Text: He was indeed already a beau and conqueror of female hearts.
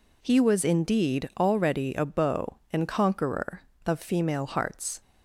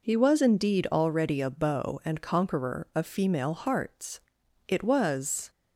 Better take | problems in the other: first | goes on to say "It was"; noticeable; from 4.6 s on; 0.82 s long

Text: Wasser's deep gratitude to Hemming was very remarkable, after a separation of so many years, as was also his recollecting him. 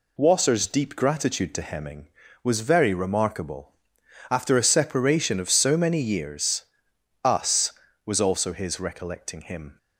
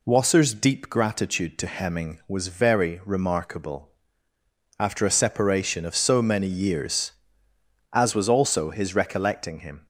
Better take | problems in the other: second | says "us" for "as"; at 7.2 s

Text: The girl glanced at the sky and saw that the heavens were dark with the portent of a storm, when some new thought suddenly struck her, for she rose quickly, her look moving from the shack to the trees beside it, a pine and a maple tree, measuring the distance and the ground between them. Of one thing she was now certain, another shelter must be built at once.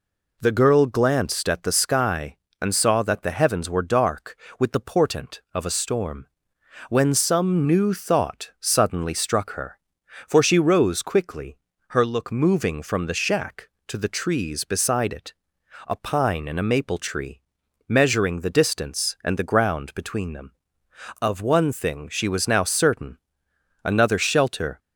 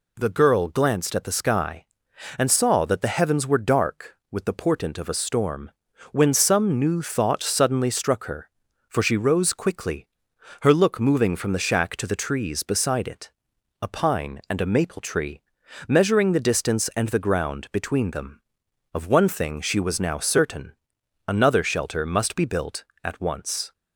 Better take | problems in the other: second | stops before "must be built at once"; at 24.7 s

